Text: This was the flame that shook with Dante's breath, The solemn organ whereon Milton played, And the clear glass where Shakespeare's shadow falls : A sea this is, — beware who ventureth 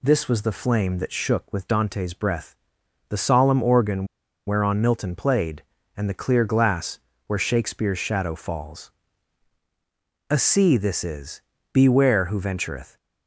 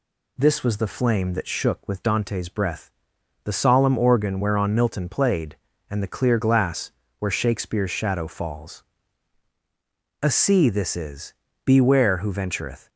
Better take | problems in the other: second | pauses between "organ" and "whereon"; at 4.0 s; 0.40 s long // pauses between "glass" and "where"; slight; at 6.9 s; 0.30 s long; slight in the second

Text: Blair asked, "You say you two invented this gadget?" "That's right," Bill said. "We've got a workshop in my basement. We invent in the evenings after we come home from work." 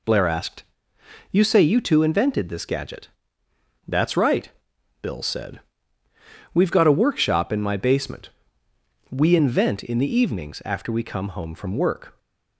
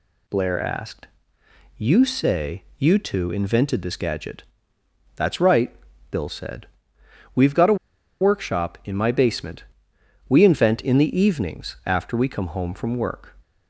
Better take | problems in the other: first | pauses between "a" and "workshop"; noticeable; at 7.7 s; 0.46 s long

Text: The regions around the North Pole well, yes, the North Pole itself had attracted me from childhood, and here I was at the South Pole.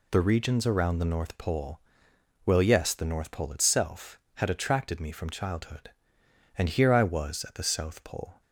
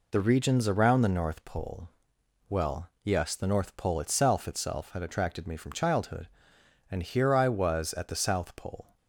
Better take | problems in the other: first | pauses between "Pole" and "well"; noticeable; at 1.8 s; 0.60 s long; noticeable in the first // says "itself" twice; at 4.4 s

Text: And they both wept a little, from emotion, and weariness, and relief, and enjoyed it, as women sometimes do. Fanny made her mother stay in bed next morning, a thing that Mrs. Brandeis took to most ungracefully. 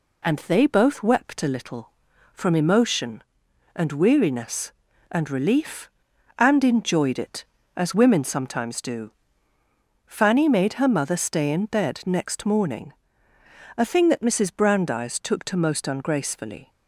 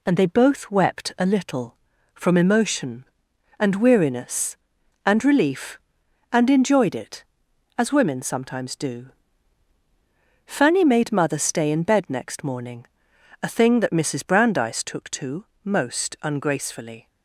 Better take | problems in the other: first | skips "her"; at 11.1 s // pauses between "to" and "most"; slight; at 15.4 s; 0.20 s long

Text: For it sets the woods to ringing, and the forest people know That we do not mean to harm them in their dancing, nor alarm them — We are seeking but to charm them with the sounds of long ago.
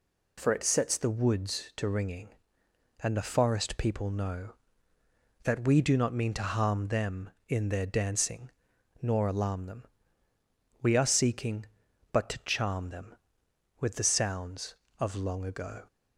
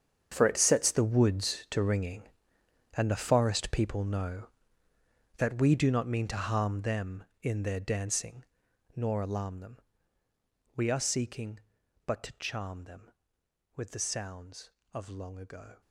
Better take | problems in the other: first | gets quieter; strong; throughout; 15 dB

